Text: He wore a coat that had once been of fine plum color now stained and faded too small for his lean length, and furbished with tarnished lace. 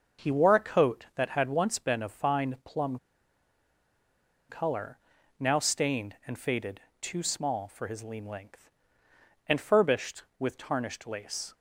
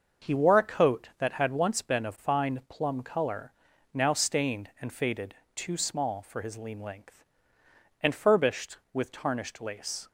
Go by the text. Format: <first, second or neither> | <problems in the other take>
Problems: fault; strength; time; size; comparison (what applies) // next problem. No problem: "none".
second | starts louder than the rest; until 1.3 s; 6 dB; also in the second // pauses between "plum" and "color"; strong; at 2.9 s; 1.5 s long // pauses between "color" and "now"; at 4.9 s; 0.40 s long; also in the second // pauses between "faded" and "too"; slight; at 6.7 s; 0.20 s long; slight in the second